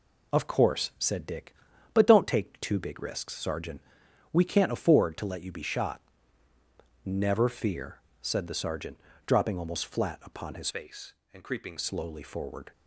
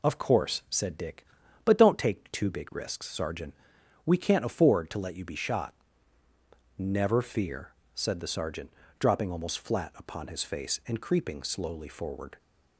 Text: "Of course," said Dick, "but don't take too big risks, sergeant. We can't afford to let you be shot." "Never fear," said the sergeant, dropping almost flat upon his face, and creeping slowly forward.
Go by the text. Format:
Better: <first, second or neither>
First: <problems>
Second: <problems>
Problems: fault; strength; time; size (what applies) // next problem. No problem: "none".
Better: second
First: changes voice from "face" to "creeping"; from 10.6 to 11.7 s; 1.1 s long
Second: none